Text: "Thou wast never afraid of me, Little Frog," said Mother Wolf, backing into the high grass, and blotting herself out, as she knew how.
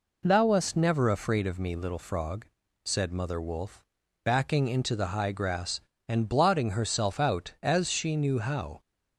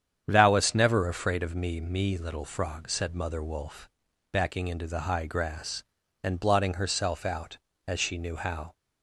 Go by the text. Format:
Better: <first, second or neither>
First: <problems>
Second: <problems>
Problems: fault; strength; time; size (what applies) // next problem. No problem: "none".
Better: first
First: none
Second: starts louder than the rest; strong; until 1.2 s; 8.5 dB // says "me" twice; at 1.8 s